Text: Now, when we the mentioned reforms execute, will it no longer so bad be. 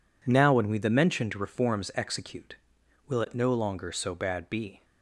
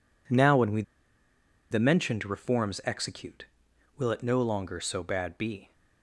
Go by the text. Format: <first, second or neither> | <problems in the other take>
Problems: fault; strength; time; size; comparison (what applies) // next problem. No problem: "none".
first | pauses between "we" and "the"; noticeable; at 0.8 s; 0.88 s long